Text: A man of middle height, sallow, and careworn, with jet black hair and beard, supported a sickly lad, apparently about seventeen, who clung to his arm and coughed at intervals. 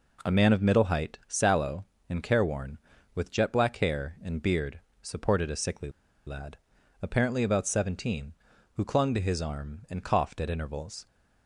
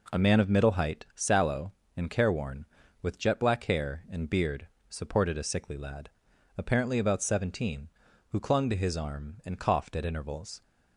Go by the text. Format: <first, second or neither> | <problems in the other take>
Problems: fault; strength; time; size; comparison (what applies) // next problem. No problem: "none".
second | pauses between "sickly" and "lad"; at 5.8 s; 0.37 s long